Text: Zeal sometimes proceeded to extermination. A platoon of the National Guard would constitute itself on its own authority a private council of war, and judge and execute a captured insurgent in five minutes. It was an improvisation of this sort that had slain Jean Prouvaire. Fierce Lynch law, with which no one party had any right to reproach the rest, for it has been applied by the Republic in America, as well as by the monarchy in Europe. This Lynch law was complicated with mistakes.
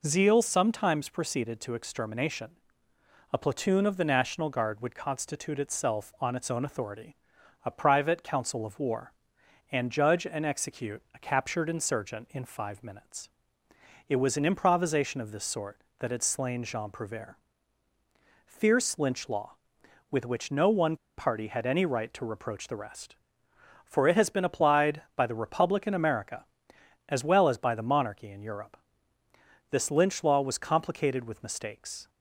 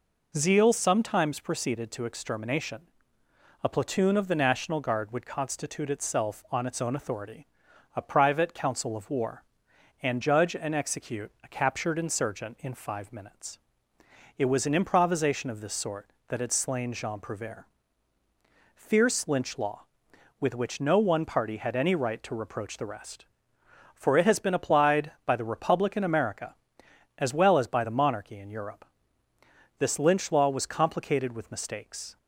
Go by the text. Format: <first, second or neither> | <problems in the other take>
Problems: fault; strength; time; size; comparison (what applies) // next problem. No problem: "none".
second | pauses between "authority" and "a"; noticeable; at 7.1 s; 0.50 s long; noticeable in the second // pauses between "one" and "party"; slight; at 20.9 s; 0.22 s long